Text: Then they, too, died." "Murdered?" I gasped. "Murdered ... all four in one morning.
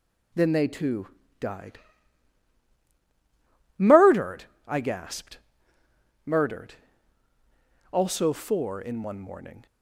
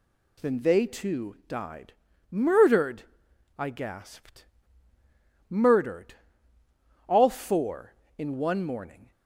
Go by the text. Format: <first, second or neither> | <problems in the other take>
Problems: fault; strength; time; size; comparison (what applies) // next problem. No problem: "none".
second | says "also" for "all"; at 7.9 s